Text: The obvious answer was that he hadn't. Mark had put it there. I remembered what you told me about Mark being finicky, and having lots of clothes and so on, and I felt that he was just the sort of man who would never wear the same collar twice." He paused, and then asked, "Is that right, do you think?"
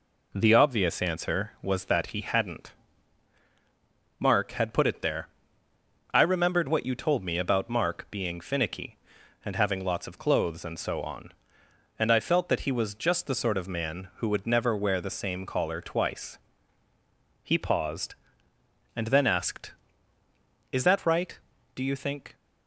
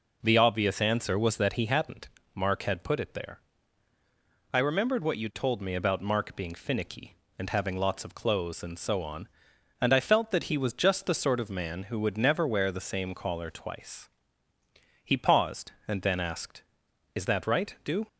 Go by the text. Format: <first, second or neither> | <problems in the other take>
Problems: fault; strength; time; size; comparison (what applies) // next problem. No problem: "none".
first | stops before "you think"; at 18.0 s